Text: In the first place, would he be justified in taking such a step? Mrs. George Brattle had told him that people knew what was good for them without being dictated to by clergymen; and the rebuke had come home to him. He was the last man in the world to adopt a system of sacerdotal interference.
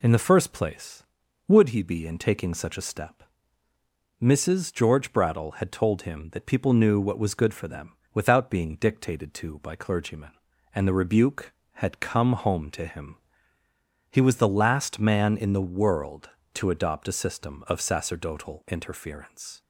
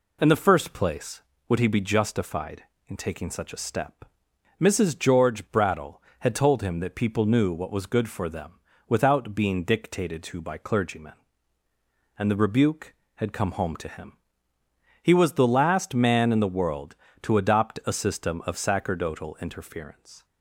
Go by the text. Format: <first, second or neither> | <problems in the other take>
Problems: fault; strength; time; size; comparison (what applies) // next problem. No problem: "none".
second | skips "justified"; at 2.0 s // pauses between "them" and "without"; slight; at 7.9 s; 0.22 s long; slight in the second